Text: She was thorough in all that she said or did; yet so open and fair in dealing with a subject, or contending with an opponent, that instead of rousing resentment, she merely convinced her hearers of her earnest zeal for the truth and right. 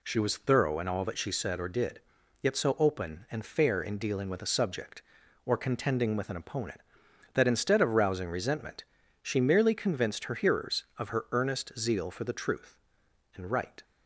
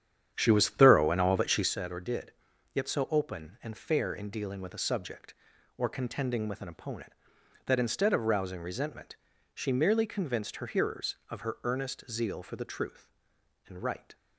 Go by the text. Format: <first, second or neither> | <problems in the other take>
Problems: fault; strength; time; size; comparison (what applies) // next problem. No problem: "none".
first | starts louder than the rest; strong; until 1.7 s; 9 dB